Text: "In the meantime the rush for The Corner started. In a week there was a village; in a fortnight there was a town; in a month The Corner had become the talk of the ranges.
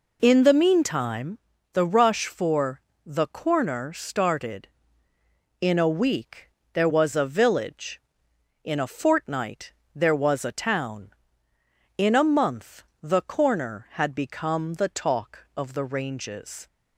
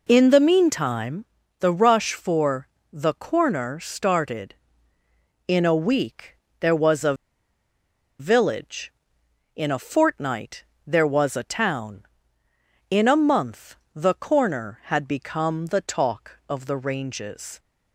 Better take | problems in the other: first | pauses between "meantime" and "the"; slight; at 1.2 s; 0.34 s long; slight in the first // pauses between "for" and "The"; slight; at 2.6 s; 0.24 s long; slight in the first // pauses between "week" and "there"; slight; at 6.3 s; 0.24 s long; slight in the first // pauses between "a" and "village"; at 7.1 s; 1.0 s long // pauses between "fortnight" and "there"; slight; at 10.6 s; 0.24 s long; slight in the first // pauses between "month" and "The"; slight; at 13.7 s; 0.18 s long; slight in the first

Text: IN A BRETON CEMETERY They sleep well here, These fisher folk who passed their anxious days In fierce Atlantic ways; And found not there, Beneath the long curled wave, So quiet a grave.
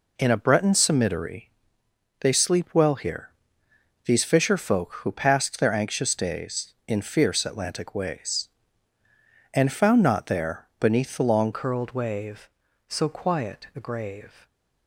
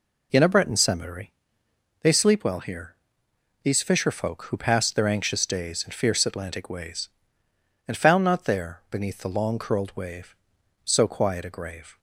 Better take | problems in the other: second | pauses between "CEMETERY" and "They"; noticeable; at 1.4 s; 0.70 s long; noticeable in the second // changes voice at "curled"; from 11.5 s on; 2.9 s long

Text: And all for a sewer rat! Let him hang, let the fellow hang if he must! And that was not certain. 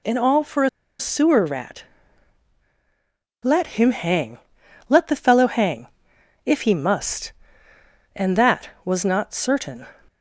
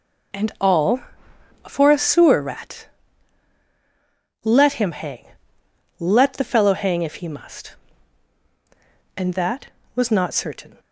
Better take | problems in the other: second | pauses between "a" and "sewer"; slight; at 0.6 s; 0.31 s long // pauses between "hang" and "if"; noticeable; at 5.8 s; 0.58 s long

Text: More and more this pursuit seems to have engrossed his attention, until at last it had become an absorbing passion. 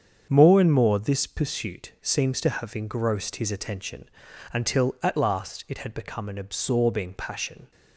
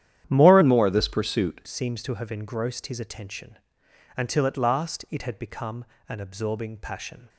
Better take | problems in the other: first | starts louder than the rest; strong; until 1.3 s; 10.5 dB; strong in the first // changes voice from "and" to "pursuit"; from 0.6 to 1.5 s; 0.9 s long // pauses between "become" and "an"; slight; at 5.8 s; 0.24 s long

